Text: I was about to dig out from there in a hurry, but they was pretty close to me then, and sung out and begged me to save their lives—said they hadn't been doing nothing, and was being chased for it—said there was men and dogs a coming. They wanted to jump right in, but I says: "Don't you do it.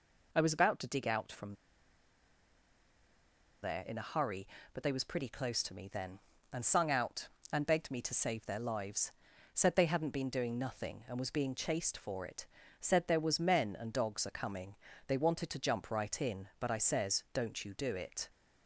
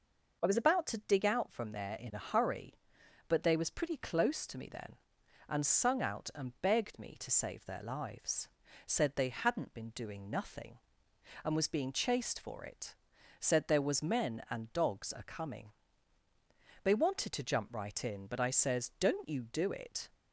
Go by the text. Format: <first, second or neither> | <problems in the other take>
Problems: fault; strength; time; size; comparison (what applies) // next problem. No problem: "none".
second | pauses between "from" and "there"; strong; at 1.5 s; 2.0 s long